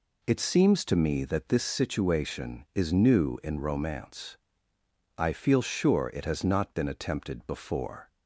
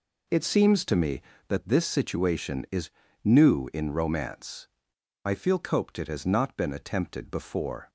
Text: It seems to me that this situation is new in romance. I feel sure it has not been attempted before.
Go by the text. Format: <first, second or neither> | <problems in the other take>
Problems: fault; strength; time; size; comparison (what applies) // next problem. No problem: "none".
first | pauses between "is" and "new"; slight; at 2.8 s; 0.34 s long // says "coped" for "sure"; at 5.5 s